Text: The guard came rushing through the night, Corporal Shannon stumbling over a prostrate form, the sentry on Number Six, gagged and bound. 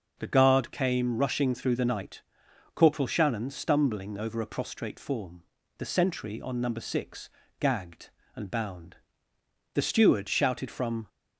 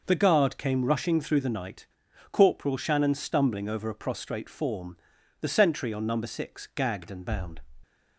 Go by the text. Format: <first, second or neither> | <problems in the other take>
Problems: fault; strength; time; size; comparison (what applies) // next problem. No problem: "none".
second | starts louder than the rest; noticeable; until 1.2 s; 6 dB // goes on to say "The steward shouted from"; from 9.7 s on; 1.3 s long